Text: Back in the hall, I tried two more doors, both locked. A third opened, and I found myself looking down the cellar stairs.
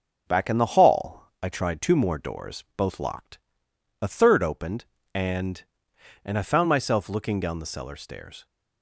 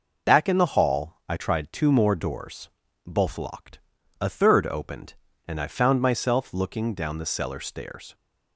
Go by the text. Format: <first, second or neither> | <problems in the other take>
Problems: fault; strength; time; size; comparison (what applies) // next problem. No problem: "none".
second | says "and" twice; at 6.2 s